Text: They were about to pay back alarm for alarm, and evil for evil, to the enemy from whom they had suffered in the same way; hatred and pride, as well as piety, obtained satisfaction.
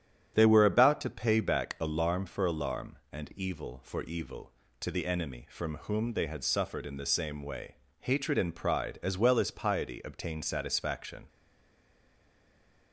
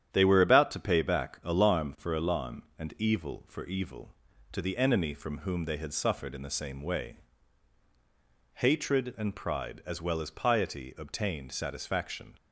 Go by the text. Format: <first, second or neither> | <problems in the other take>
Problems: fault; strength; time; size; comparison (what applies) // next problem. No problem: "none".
second | starts louder than the rest; strong; until 1.3 s; 8.5 dB; strong in the second // stays silent after the last word; noticeable; from 11.2 s on; 1.7 s long